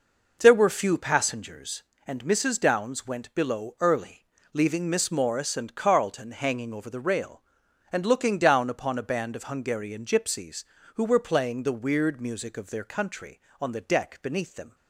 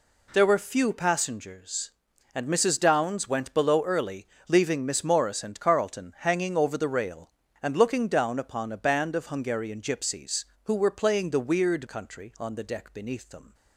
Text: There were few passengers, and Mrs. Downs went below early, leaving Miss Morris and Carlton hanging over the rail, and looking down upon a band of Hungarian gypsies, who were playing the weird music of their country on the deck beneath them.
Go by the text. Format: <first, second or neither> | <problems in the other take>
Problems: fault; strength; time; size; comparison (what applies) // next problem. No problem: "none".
first | skips "music of their"; at 11.8 s